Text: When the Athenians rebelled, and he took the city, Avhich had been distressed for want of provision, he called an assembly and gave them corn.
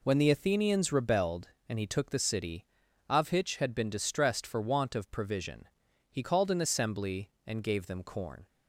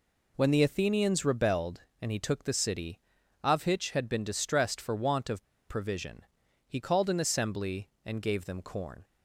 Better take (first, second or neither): first